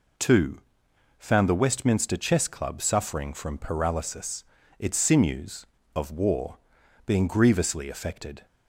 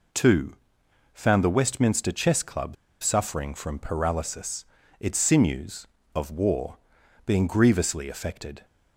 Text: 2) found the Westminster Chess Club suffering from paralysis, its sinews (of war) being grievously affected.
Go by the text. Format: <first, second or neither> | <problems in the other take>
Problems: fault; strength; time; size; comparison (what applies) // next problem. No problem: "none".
first | pauses between "Club" and "suffering"; slight; at 2.7 s; 0.27 s long